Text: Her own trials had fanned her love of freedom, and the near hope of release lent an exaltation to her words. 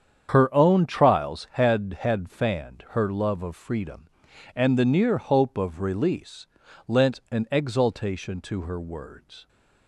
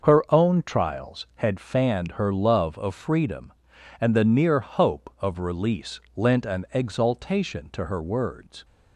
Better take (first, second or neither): second